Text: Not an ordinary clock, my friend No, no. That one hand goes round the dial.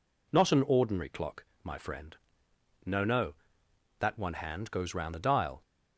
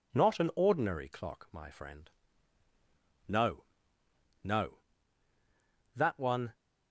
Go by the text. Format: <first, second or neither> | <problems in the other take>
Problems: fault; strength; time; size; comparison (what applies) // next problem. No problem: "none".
first | pauses between "friend" and "No"; at 2.0 s; 1.2 s long; noticeable in the first // stops before "hand goes round the dial"; at 6.5 s